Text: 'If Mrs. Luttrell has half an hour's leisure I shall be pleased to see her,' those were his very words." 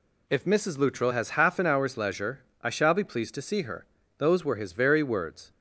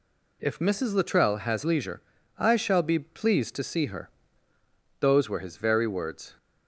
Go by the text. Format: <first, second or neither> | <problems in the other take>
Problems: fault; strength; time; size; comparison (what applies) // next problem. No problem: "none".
first | skips "half an hour's"; at 1.6 s // pauses between "leisure" and "I"; at 2.0 s; 0.38 s long; slight in the first